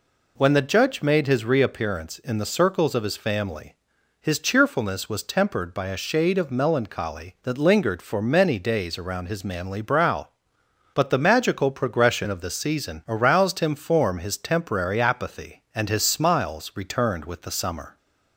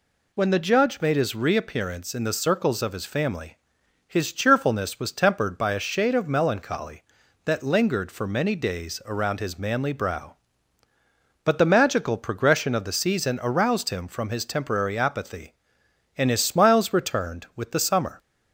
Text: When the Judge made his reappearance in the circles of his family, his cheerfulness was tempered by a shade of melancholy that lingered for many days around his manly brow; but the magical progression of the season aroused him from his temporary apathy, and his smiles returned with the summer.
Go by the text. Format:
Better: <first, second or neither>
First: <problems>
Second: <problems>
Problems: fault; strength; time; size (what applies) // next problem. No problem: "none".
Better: second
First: says "form" for "from"; at 13.7 s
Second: none